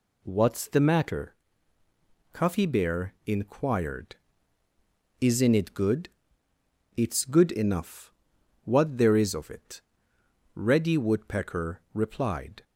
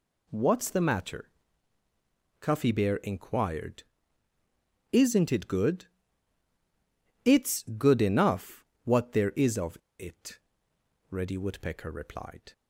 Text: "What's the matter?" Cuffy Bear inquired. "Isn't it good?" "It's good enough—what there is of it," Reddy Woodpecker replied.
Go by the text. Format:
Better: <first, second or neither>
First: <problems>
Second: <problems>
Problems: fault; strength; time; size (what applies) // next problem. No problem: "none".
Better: first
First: none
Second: pauses between "of" and "it"; slight; at 9.7 s; 0.21 s long